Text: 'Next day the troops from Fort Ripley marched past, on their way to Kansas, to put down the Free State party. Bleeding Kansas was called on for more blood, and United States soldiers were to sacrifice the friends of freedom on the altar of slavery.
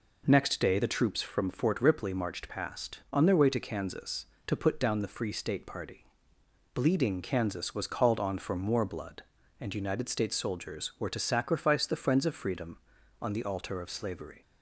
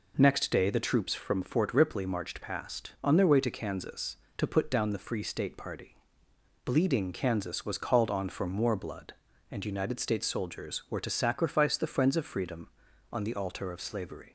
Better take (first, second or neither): neither